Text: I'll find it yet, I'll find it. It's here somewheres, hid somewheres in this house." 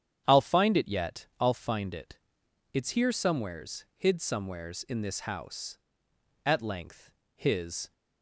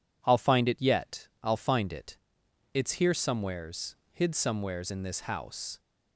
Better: second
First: starts louder than the rest; strong; until 1.2 s; 9 dB // goes on to say "At length his"; from 6.4 s on; 1.4 s long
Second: none

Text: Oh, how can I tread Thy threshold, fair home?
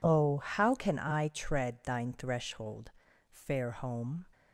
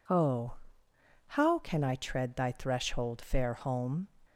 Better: second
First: says "Thine" for "Thy"; at 1.8 s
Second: none

